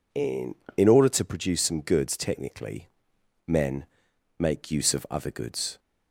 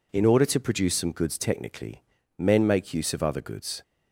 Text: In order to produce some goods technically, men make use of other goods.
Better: second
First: says "In" twice; at 0.7 s // pauses between "men" and "make"; noticeable; at 3.8 s; 0.53 s long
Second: none

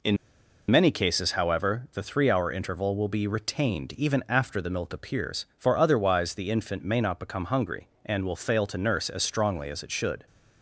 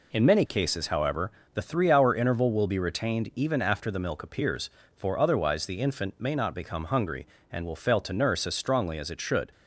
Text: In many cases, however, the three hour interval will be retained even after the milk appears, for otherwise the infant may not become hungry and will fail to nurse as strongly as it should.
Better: second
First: pauses between "In" and "many"; noticeable; at 0.1 s; 0.53 s long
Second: none

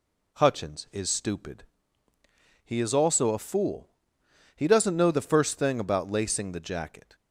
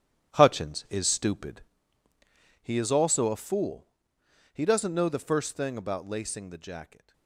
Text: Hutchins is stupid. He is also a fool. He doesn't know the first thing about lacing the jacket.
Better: first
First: none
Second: gets quieter; strong; throughout; 10 dB

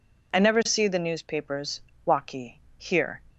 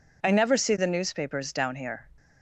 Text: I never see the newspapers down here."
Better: second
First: says "waki" for "down"; at 2.0 s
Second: none

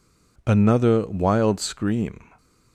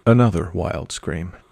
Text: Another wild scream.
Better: neither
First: none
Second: none

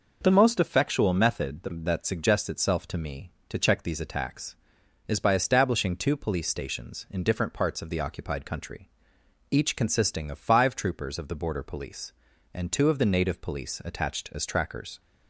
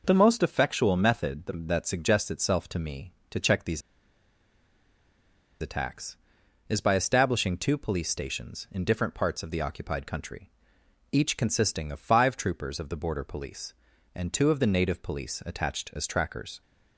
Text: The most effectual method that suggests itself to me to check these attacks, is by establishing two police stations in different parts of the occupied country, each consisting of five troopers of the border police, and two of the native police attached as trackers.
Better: first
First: none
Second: pauses between "these" and "attacks"; strong; at 3.8 s; 1.7 s long

